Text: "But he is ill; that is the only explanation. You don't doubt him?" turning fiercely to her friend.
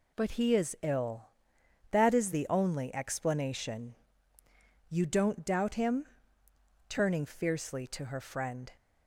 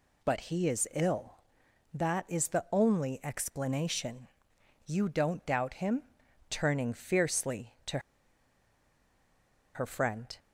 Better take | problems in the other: first | pauses between "to" and "her"; strong; at 7.9 s; 1.7 s long

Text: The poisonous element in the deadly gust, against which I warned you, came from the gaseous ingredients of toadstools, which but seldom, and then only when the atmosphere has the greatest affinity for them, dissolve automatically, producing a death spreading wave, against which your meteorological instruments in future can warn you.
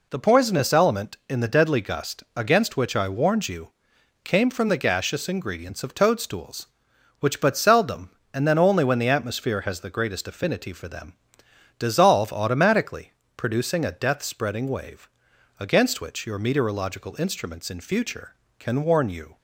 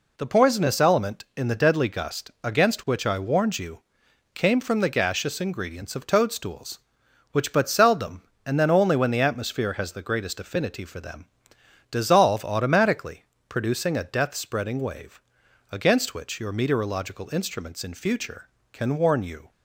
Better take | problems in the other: neither | none

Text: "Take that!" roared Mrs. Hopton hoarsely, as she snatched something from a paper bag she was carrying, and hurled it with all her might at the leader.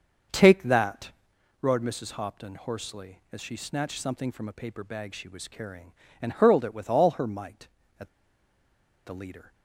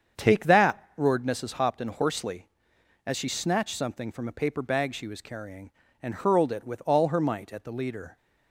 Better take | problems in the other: second | starts louder than the rest; until 1.8 s; 6.5 dB; strong in the second // pauses between "at" and "the"; noticeable; at 8.0 s; 0.97 s long

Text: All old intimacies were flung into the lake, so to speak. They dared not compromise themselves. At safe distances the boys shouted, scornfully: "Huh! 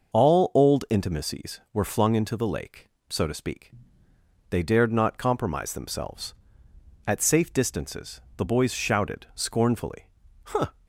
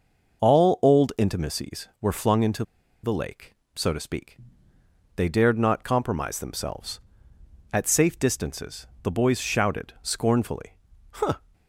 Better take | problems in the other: first | pauses between "into" and "the"; at 2.6 s; 0.39 s long // pauses between "distances" and "the"; slight; at 8.8 s; 0.16 s long; slight in the first

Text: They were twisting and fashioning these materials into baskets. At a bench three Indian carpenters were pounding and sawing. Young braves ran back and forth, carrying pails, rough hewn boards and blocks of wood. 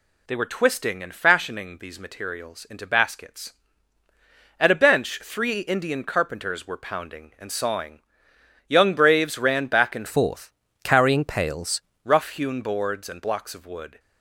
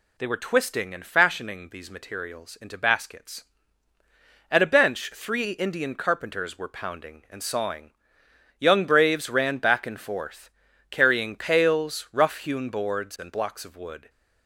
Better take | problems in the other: second | changes voice from "forth" to "pails"; from 10.0 to 11.8 s; 1.8 s long

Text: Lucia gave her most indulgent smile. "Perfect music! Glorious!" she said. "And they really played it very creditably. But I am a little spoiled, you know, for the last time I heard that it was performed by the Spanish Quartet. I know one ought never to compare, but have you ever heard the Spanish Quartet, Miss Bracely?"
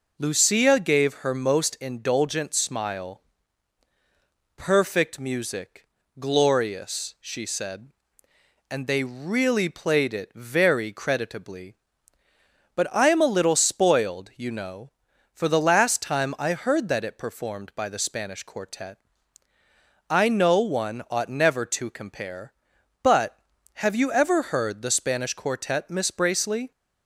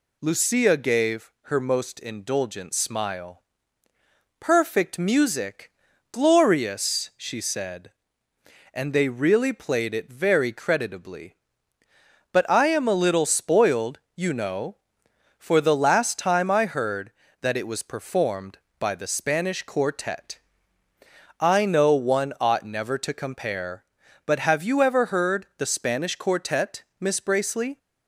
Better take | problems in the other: second | skips "was"; at 17.1 s

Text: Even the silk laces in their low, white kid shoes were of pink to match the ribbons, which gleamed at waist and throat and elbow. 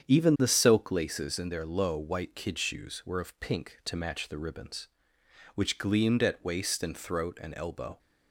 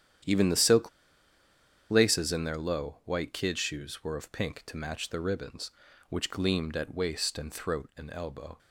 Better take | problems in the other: first | starts louder than the rest; strong; until 2.2 s; 9.5 dB; strong in the first // pauses between "silk" and "laces"; at 0.8 s; 1.0 s long

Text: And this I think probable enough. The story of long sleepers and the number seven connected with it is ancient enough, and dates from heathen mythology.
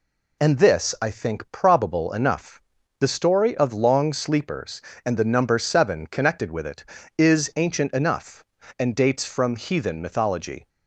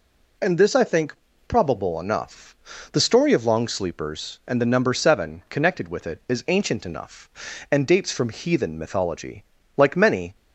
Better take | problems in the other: first | pauses between "think" and "probable"; slight; at 1.1 s; 0.32 s long // goes on to say "Like many"; from 9.7 s on; 0.58 s long

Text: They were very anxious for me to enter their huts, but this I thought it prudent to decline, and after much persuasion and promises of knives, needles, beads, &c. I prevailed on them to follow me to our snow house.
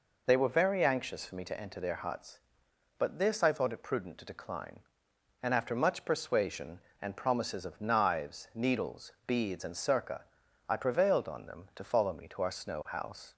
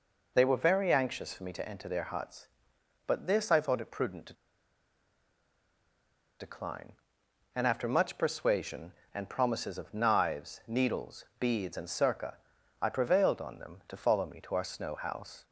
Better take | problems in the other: first | pauses between "to" and "decline"; strong; at 4.3 s; 2.0 s long

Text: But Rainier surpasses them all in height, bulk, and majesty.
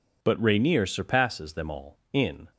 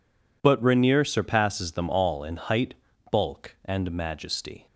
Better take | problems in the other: second | stops before "height bulk and majesty"; at 2.5 s

